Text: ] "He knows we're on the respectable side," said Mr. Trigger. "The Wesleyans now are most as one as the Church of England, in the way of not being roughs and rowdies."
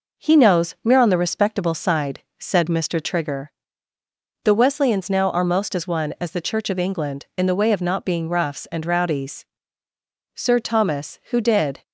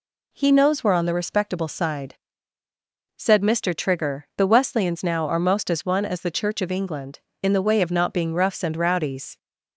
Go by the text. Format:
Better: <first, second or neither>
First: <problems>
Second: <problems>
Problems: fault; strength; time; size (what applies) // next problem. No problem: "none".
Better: second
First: goes on to say "Sir Thomas who did"; from 10.3 s on; 1.4 s long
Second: none